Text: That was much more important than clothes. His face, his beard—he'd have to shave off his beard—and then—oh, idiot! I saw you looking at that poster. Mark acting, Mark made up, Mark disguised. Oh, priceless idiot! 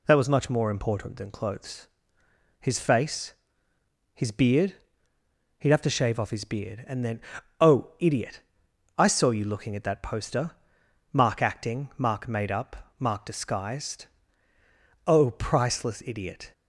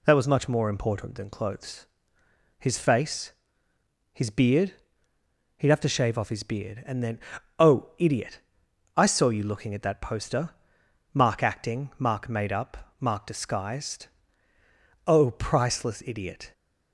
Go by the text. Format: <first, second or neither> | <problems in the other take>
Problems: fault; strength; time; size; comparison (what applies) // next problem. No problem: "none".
neither | none